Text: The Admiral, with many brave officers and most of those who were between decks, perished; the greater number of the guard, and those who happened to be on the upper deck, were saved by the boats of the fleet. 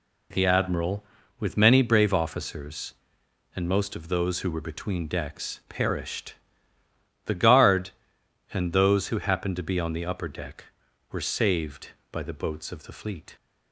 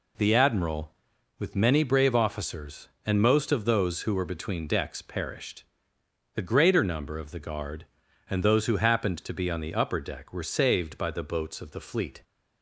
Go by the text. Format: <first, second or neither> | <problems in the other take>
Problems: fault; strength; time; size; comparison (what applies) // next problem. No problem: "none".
second | skips "greater number of the"; at 7.3 s